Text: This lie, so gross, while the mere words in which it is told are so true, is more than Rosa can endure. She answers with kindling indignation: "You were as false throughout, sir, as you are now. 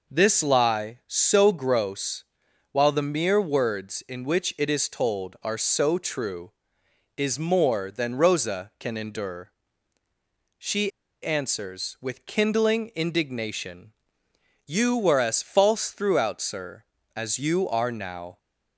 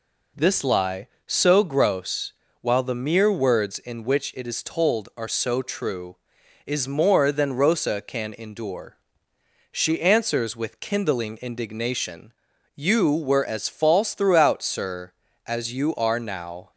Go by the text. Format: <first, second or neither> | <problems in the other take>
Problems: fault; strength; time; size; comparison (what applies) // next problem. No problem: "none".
second | pauses between "She" and "answers"; slight; at 10.9 s; 0.34 s long